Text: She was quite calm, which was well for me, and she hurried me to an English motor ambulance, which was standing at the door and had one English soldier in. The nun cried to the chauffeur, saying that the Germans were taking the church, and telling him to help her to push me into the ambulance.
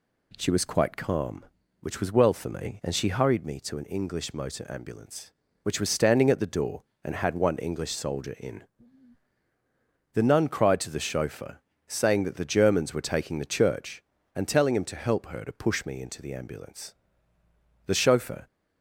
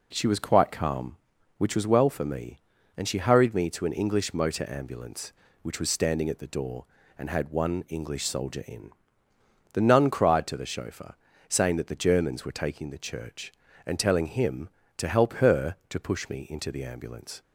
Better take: second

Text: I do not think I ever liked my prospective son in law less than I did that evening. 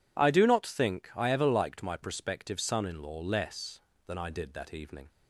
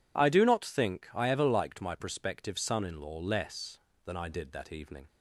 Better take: neither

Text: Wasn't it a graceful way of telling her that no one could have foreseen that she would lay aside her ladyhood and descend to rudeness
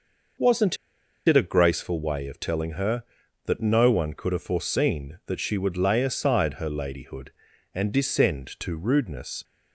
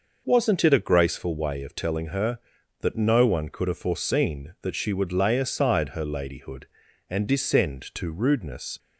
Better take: second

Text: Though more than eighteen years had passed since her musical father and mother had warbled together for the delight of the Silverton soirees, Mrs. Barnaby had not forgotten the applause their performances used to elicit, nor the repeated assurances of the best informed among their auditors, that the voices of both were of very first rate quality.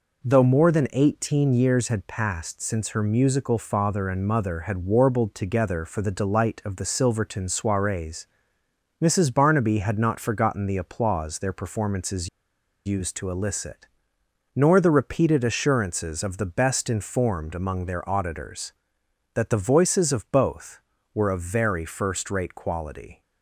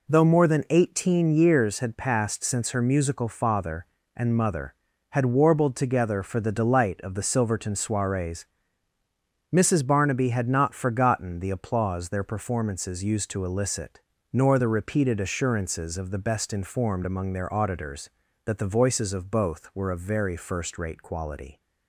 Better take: second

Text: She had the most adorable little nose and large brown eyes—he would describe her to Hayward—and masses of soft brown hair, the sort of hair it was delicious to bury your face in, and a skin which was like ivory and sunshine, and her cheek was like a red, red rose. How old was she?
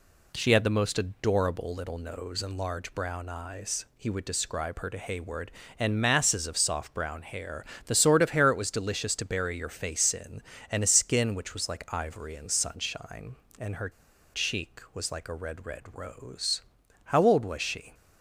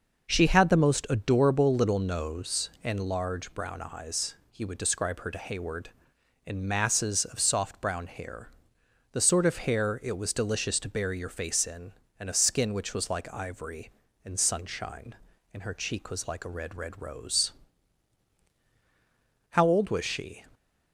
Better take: second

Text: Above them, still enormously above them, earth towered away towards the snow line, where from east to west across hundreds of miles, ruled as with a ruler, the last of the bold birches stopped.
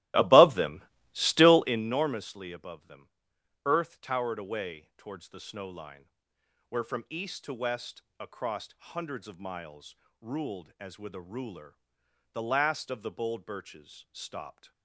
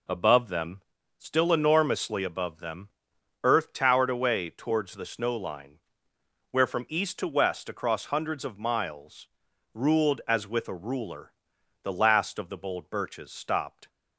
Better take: second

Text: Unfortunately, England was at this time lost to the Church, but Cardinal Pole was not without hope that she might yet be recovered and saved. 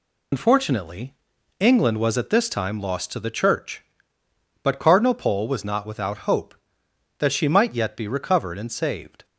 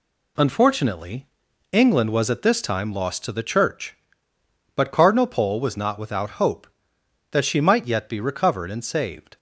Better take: second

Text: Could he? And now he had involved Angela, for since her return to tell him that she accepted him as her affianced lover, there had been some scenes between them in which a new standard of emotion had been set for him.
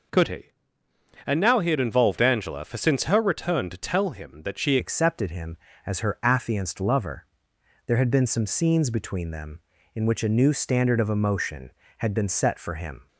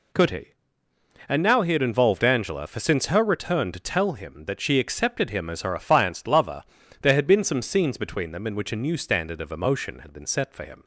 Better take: second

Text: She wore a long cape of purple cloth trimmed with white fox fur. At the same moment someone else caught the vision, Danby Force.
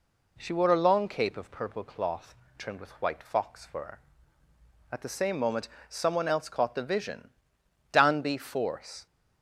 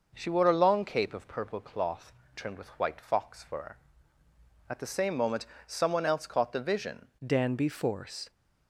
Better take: first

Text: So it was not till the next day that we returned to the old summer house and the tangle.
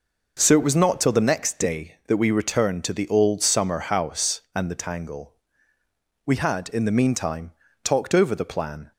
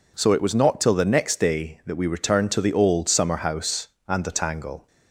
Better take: second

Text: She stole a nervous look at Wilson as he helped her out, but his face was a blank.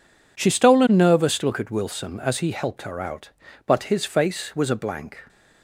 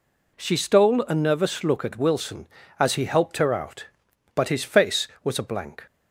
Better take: neither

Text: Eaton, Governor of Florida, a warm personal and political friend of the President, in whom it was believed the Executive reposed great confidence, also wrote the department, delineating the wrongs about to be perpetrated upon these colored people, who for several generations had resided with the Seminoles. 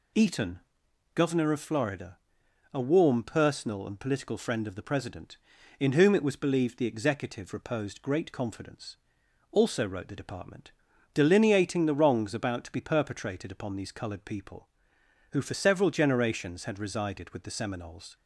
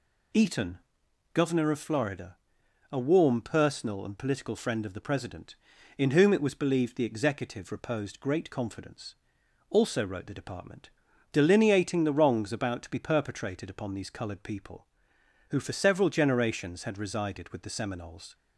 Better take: neither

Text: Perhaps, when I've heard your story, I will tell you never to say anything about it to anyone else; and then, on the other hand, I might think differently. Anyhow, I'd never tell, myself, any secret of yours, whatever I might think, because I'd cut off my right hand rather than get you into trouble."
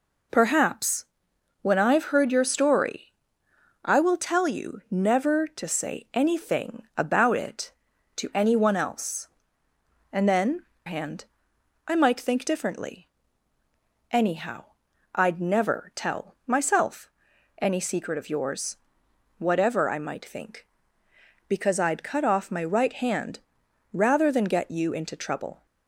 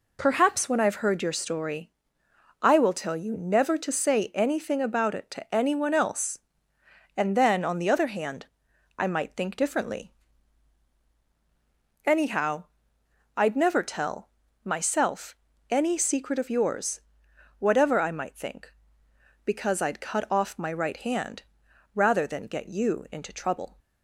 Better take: second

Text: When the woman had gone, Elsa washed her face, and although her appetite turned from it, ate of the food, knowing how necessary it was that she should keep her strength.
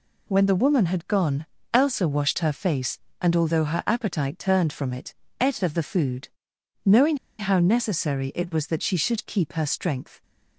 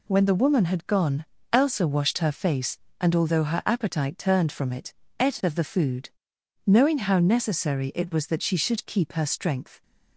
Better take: second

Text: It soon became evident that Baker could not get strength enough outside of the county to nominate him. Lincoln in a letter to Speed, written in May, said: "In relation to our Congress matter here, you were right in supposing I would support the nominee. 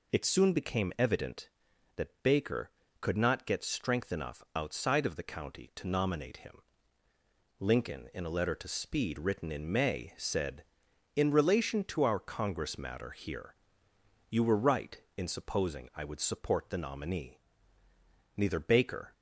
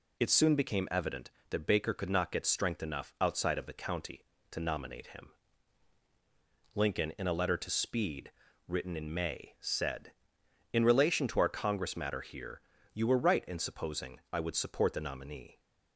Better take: second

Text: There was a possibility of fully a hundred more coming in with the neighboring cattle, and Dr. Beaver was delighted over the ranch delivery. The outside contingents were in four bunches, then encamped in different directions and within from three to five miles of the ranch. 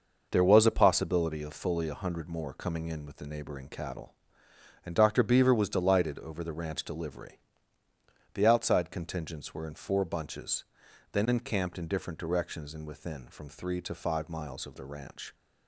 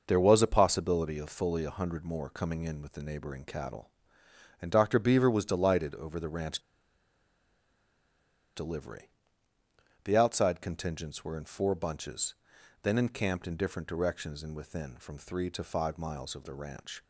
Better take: first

